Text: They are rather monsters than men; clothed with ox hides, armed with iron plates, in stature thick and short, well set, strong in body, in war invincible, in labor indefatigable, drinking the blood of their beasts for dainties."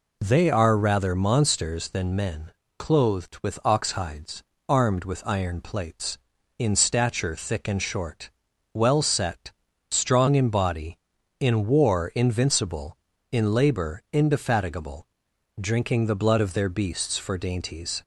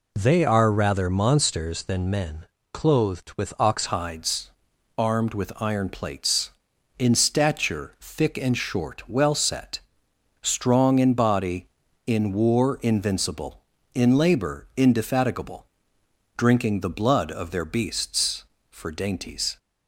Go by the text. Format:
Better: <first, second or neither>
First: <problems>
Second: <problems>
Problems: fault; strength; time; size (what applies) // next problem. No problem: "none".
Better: first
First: none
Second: changes voice at "hides"; from 3.8 s on; 15.7 s long